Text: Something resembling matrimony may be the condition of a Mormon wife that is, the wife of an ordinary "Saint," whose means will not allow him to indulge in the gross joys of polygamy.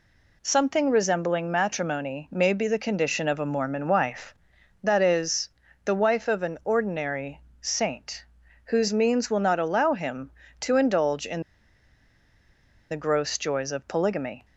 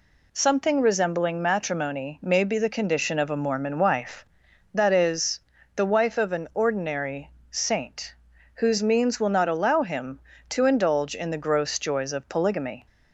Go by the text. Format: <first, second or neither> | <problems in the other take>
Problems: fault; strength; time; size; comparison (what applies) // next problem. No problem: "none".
second | pauses between "ordinary" and "Saint"; slight; at 7.4 s; 0.20 s long; slight in the second // pauses between "in" and "the"; strong; at 11.4 s; 1.4 s long